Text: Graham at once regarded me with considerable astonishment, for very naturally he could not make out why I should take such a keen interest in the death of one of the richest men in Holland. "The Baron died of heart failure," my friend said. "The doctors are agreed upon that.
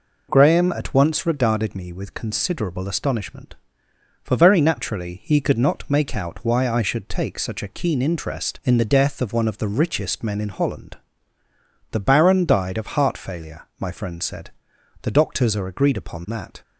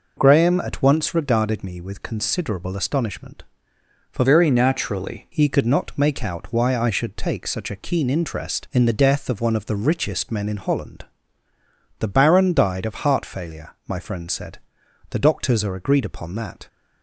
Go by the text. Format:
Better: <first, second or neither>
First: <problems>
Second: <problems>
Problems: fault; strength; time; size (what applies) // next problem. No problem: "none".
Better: first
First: none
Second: changes voice from "very" to "naturally"; from 4.2 to 5.2 s; 1.0 s long